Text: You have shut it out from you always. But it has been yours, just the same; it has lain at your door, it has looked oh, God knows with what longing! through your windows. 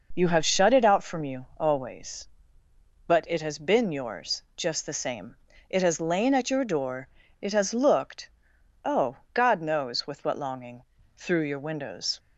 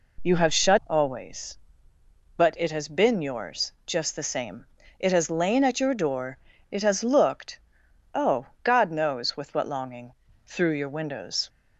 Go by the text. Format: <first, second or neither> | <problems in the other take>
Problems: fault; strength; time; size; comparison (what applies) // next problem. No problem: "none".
first | skips "it out from you"; at 0.8 s // pauses between "looked" and "oh"; noticeable; at 7.5 s; 0.56 s long; noticeable in the first